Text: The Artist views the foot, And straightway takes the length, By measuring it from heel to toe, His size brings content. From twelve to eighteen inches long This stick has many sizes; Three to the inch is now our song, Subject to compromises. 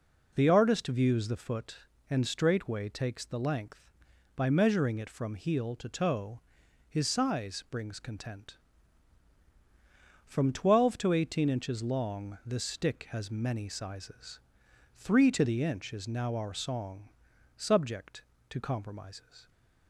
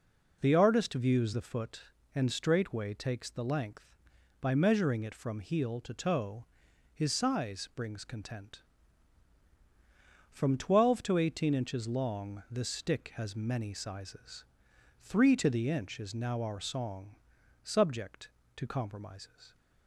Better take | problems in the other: neither | none

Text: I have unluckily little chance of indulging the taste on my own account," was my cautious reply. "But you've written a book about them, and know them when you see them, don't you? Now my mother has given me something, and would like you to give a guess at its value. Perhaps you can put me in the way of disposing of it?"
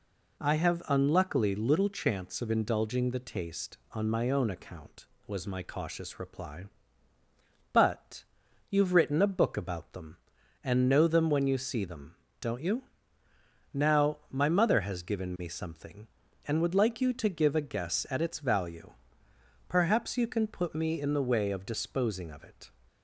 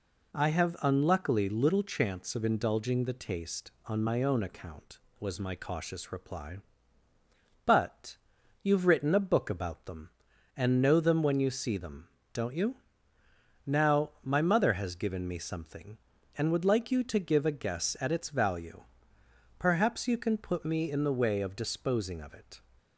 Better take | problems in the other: neither | pauses between "But" and "you've"; noticeable; the same in both

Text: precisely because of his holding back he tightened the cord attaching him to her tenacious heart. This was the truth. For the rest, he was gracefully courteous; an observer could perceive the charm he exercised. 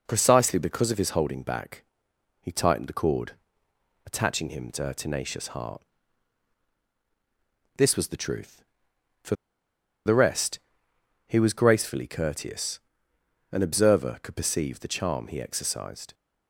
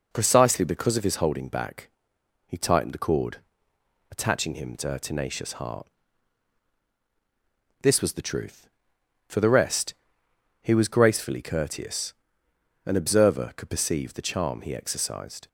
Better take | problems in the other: second | pauses between "back" and "he"; noticeable; at 1.8 s; 0.58 s long; noticeable in the second // pauses between "cord" and "attaching"; noticeable; at 3.3 s; 0.74 s long; noticeable in the second // pauses between "For" and "the"; noticeable; at 9.3 s; 0.72 s long

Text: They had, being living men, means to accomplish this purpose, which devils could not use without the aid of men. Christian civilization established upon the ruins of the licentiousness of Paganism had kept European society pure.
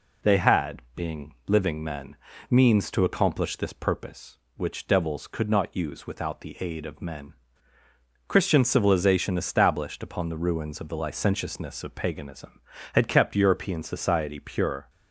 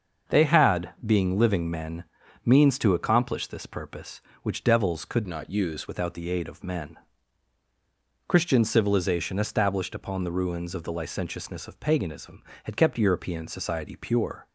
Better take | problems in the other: first | starts louder than the rest; until 1.4 s; 6.5 dB // changes voice from "not" to "use"; from 5.2 to 5.8 s; 0.6 s long

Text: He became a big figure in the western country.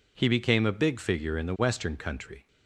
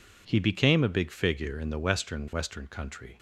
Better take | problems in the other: first | says "western" twice; at 2.3 s

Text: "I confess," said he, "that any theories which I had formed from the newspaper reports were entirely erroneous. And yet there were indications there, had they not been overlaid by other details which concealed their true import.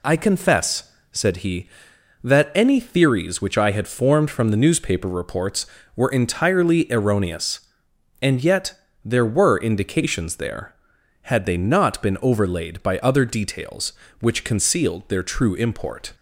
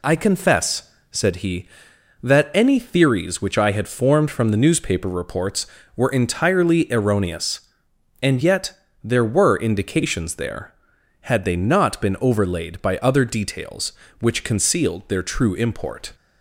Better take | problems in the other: neither | pauses between "yet" and "there"; slight; the same in both

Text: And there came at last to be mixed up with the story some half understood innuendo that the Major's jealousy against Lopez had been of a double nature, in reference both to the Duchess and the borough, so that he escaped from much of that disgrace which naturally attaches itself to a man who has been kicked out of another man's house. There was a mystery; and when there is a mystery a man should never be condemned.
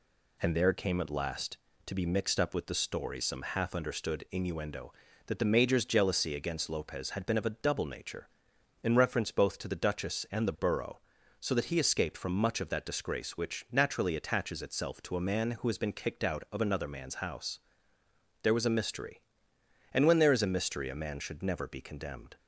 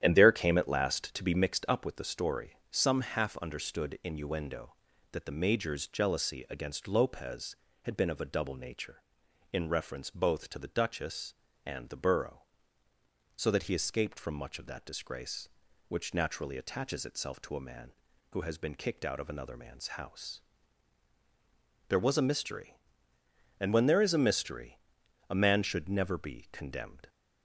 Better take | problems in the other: first | starts louder than the rest; strong; until 1.5 s; 11 dB // pauses between "story" and "some"; slight; at 2.5 s; 0.18 s long // pauses between "mystery" and "a"; noticeable; at 24.7 s; 0.50 s long

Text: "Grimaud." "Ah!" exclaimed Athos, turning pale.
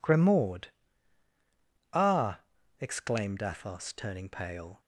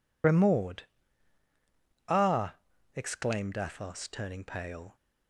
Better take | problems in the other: first | loses the start of "Grimaud"; at 0.2 s; 70 ms

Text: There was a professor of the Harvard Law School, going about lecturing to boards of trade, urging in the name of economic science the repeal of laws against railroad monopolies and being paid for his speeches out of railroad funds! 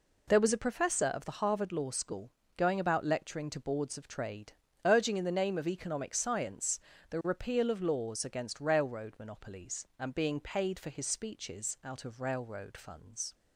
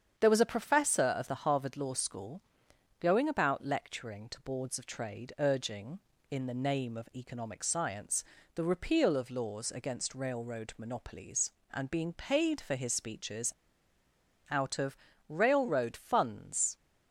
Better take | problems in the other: first | starts louder than the rest; strong; until 1.1 s; 8 dB // pauses between "science" and "the"; slight; at 8.2 s; 0.32 s long; slight in the first // pauses between "speeches" and "out"; at 13.5 s; 0.98 s long // pauses between "of" and "railroad"; slight; at 14.9 s; 0.32 s long

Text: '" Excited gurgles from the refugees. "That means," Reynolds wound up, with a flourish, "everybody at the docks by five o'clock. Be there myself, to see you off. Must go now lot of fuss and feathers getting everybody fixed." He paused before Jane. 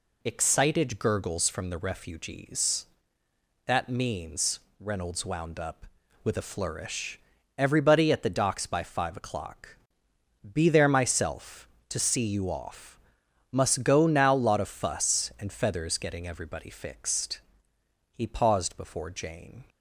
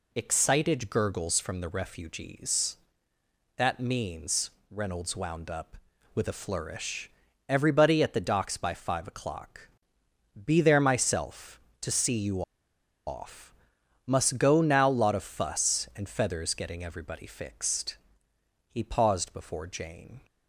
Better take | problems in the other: first | pauses between "you" and "off"; noticeable; at 12.4 s; 0.64 s long

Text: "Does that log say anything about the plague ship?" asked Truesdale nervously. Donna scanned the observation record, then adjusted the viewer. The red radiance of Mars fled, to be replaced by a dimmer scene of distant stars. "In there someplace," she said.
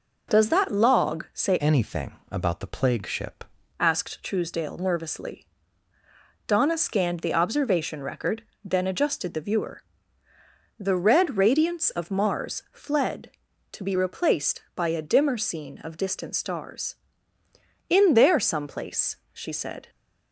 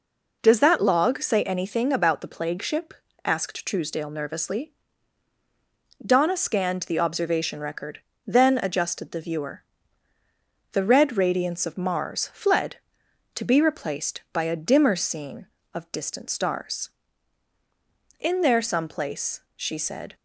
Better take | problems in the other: second | changes voice from "anything" to "ship"; from 1.6 to 3.4 s; 1.8 s long

